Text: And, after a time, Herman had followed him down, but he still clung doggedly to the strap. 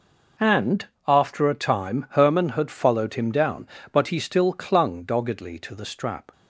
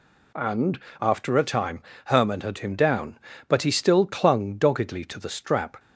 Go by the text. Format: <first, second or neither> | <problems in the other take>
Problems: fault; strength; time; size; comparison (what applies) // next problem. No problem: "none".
first | skips "followed"; at 2.5 s